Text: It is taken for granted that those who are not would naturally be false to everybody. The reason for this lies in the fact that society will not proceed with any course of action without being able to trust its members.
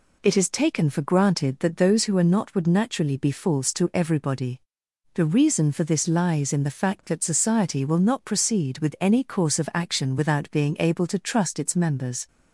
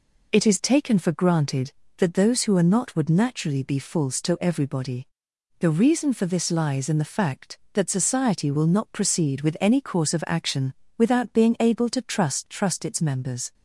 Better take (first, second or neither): first